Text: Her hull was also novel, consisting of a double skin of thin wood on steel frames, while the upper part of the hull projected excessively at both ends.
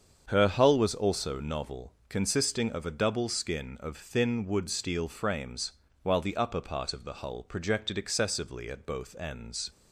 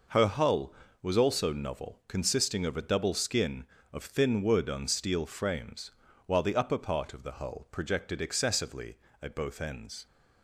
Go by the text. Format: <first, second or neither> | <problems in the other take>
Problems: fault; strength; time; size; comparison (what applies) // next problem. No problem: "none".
second | starts louder than the rest; strong; until 1.3 s; 7 dB // skips "on"; at 4.7 s